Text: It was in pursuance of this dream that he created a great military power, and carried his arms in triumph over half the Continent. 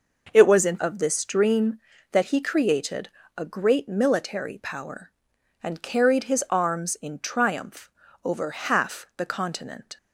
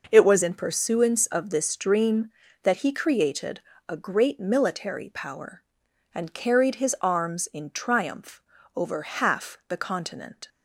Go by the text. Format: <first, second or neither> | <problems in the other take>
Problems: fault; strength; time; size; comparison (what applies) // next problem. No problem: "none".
second | skips "pursuance"; at 0.7 s // pauses between "created" and "a"; slight; at 3.0 s; 0.28 s long; slight in the second // pauses between "triumph" and "over"; slight; at 7.9 s; 0.34 s long; slight in the second